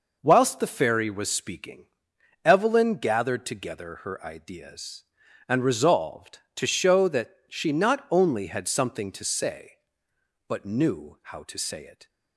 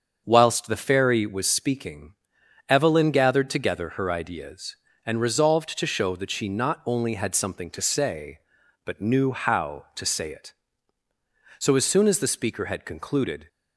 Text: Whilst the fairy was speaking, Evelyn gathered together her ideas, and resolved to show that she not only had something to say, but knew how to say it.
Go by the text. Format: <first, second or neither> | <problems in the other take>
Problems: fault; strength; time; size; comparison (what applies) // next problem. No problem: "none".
first | starts louder than the rest; until 1.2 s; 6.5 dB // goes on to say "So as soon as the speaker had concluded"; strong; from 11.5 s on; 1.9 s long